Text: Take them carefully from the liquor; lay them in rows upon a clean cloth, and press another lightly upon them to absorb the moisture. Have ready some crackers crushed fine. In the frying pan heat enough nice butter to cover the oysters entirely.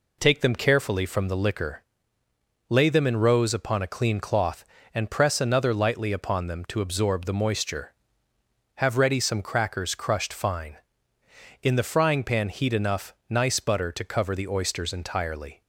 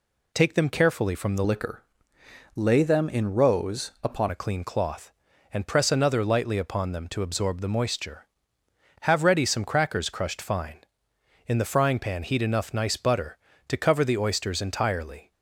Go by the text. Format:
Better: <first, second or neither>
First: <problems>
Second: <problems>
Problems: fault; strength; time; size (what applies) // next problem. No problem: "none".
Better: first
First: none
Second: changes voice from "liquor" to "upon"; from 1.4 to 4.2 s; 2.8 s long